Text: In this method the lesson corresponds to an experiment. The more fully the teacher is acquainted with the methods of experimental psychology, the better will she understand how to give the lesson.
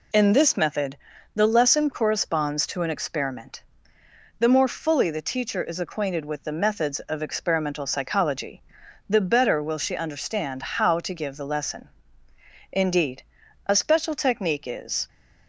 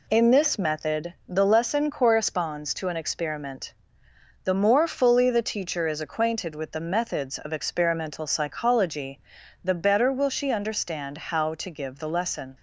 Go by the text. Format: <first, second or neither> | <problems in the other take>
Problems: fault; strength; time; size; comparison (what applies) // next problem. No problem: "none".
second | pauses between "method" and "the"; at 0.9 s; 0.38 s long // goes on to say "Indeed a special technique is"; strong; from 12.7 s on; 2.3 s long